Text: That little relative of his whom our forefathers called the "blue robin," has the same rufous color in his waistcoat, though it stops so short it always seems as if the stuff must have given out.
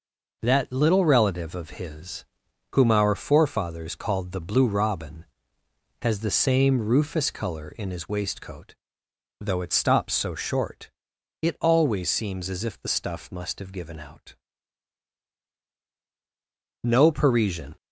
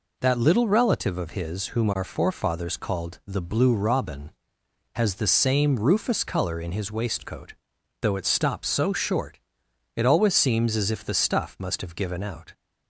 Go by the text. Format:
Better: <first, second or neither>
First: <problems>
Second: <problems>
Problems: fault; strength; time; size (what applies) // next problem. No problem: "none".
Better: second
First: pauses between "his" and "whom"; noticeable; at 2.2 s; 0.48 s long // pauses between "short" and "it"; noticeable; at 10.9 s; 0.50 s long // goes on to say "No Parisian"; noticeable; from 16.8 s on; 0.92 s long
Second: pauses between "short" and "it"; noticeable; at 9.3 s; 0.56 s long